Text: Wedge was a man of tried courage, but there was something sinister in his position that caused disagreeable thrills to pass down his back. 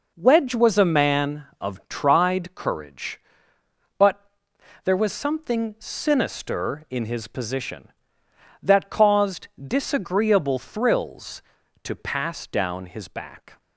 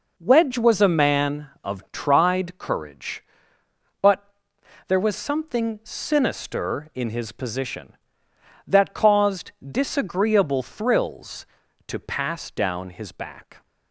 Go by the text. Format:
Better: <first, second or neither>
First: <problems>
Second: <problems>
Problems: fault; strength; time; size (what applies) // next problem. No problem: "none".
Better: neither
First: pauses between "but" and "there"; noticeable; at 4.1 s; 0.64 s long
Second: pauses between "but" and "there"; noticeable; at 4.2 s; 0.64 s long